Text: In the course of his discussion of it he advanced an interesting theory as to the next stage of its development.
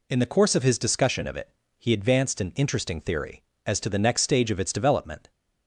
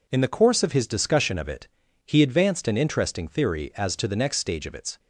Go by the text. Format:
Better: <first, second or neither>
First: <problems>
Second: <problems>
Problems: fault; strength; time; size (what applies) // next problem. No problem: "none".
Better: first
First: pauses between "it" and "he"; slight; at 1.5 s; 0.28 s long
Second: pauses between "it" and "he"; at 1.6 s; 0.38 s long // stops before "development"; at 4.9 s